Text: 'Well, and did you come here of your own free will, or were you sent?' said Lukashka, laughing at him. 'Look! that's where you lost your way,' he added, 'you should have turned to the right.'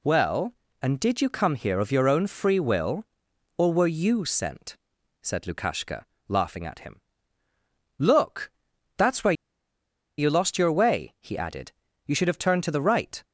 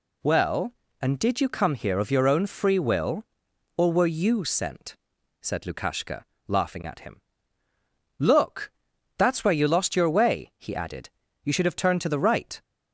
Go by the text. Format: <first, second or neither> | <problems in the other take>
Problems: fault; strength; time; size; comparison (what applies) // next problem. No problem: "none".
second | pauses between "where" and "you"; noticeable; at 9.3 s; 0.85 s long